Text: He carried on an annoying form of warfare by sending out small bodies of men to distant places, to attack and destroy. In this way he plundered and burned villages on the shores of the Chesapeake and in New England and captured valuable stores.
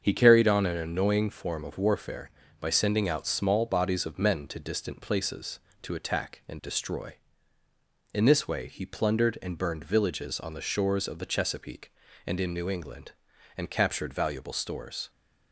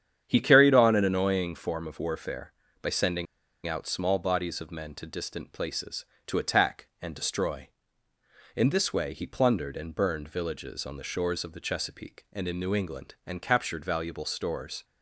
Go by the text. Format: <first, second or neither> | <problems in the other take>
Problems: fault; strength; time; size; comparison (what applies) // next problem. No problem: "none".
first | starts louder than the rest; strong; until 1.2 s; 8.5 dB; also in the first // pauses between "sending" and "out"; at 3.2 s; 0.40 s long